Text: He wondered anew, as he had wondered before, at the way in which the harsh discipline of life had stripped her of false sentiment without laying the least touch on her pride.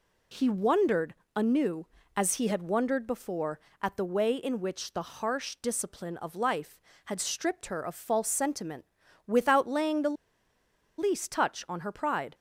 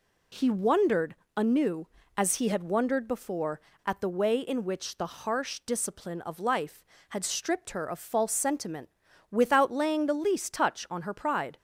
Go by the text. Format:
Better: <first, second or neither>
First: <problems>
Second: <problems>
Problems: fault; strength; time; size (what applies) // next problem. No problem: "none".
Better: second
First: pauses between "wondered" and "anew"; slight; at 1.1 s; 0.24 s long // pauses between "sentiment" and "without"; at 8.8 s; 0.40 s long // pauses between "the" and "least"; noticeable; at 10.1 s; 0.82 s long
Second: pauses between "wondered" and "anew"; slight; at 1.1 s; 0.24 s long // pauses between "sentiment" and "without"; at 8.9 s; 0.40 s long